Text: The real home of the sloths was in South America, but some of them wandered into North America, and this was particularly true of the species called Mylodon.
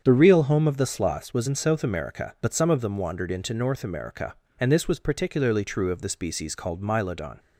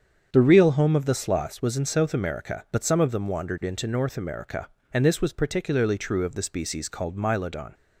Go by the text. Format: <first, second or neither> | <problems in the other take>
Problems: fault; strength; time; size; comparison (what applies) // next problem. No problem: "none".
neither | starts louder than the rest; strong; the same in both